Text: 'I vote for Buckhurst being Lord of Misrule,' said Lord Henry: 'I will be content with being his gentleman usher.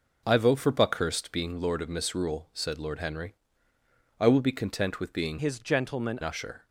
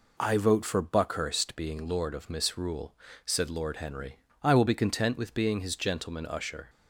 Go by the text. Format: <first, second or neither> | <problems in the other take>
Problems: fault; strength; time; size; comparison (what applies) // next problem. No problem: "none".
second | changes voice from "his" to "gentleman"; from 5.3 to 6.1 s; 0.8 s long